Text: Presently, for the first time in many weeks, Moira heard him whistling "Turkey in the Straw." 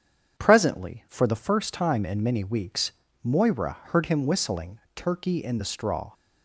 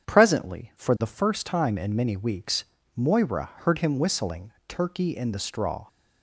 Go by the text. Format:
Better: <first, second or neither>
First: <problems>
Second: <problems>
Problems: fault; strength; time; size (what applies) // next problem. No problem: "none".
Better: neither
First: starts louder than the rest; strong; until 1.4 s; 8 dB // pauses between "whistling" and "Turkey"; slight; at 4.7 s; 0.16 s long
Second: starts louder than the rest; strong; until 1.1 s; 8 dB // pauses between "whistling" and "Turkey"; slight; at 4.5 s; 0.16 s long